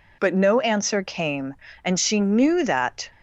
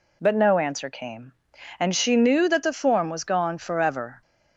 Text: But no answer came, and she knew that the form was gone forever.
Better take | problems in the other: second | stops before "the form was gone forever"; at 3.1 s

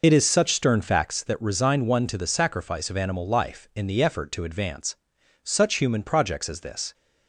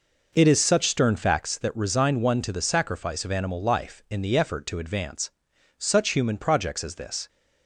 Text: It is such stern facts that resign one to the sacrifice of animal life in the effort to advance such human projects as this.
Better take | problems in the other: second | loses the start of "It"; at 0.0 s; 45 ms // pauses between "advance" and "such"; noticeable; at 4.9 s; 0.48 s long; noticeable in the second

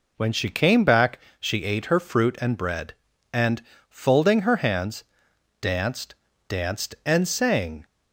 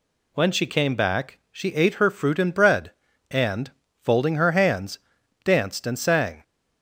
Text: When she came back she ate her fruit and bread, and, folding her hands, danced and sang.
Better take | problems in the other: second | pauses between "back" and "she"; slight; at 1.1 s; 0.22 s long // says "danced" twice; at 6.4 s

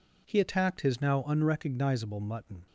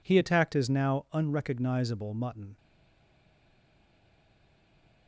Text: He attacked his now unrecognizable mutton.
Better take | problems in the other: first | stays silent after the last word; from 2.5 s on; 2.5 s long

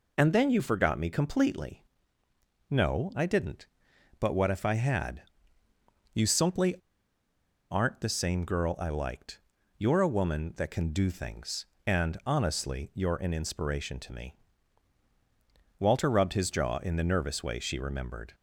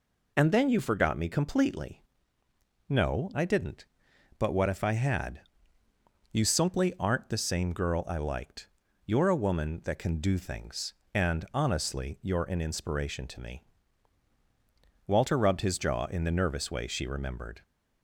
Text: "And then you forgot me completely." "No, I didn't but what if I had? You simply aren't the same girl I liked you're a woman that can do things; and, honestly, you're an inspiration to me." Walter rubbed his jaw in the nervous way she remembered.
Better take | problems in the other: second | pauses between "simply" and "aren't"; noticeable; at 6.7 s; 0.95 s long // pauses between "liked" and "you're"; at 9.4 s; 0.38 s long; also in the second

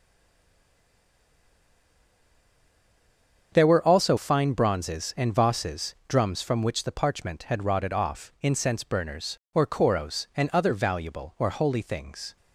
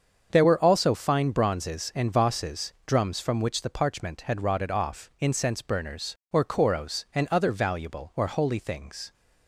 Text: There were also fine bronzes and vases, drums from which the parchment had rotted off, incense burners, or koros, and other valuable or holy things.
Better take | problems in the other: second | stays silent before the first word; strong; until 3.5 s; 3.5 s long // starts louder than the rest; until 4.5 s; 7 dB; also in the second

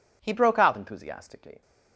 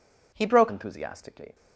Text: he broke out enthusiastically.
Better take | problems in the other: first | skips "out"; at 0.6 s

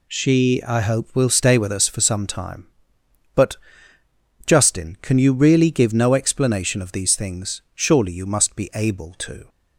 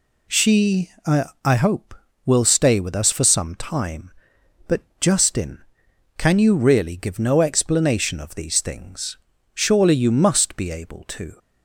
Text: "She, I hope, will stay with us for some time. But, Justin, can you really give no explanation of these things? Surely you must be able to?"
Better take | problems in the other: first | says "I" twice; at 1.4 s

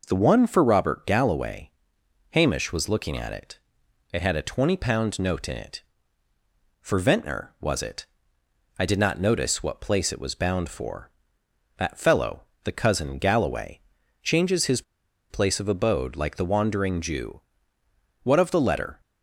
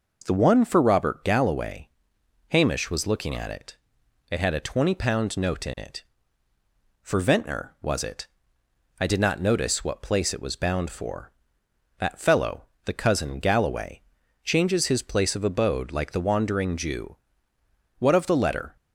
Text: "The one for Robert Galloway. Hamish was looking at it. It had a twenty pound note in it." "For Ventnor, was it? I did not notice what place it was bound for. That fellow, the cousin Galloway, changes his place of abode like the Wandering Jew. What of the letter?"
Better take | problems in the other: second | pauses between "his" and "place"; noticeable; at 14.8 s; 0.47 s long

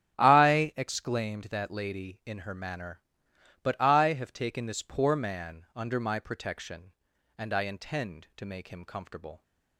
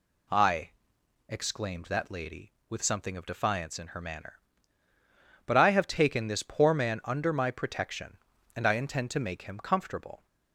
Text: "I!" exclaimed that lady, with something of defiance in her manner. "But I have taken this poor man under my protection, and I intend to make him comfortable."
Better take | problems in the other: second | starts louder than the rest; strong; until 1.1 s; 10 dB // skips "with something of defiance"; at 2.2 s

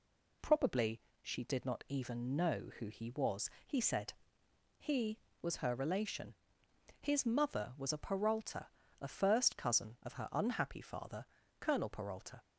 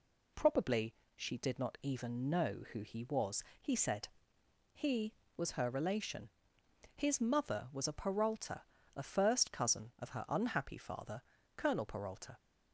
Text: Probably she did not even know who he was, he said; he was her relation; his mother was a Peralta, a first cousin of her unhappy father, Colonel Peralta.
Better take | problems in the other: neither | pauses between "Probably" and "she"; slight; the same in both

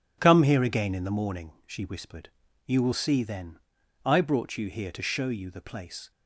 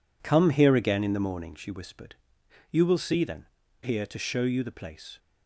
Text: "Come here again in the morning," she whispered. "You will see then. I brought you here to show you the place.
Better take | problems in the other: first | skips "I brought you"; at 3.6 s

